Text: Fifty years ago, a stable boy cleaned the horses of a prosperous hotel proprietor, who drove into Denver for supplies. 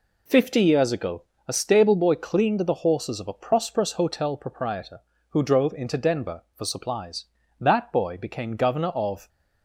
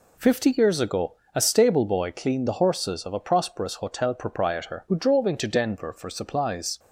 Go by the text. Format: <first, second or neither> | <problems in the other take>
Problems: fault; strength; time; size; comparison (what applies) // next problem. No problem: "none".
second | goes on to say "That boy became Governor of"; strong; from 7.6 s on; 1.6 s long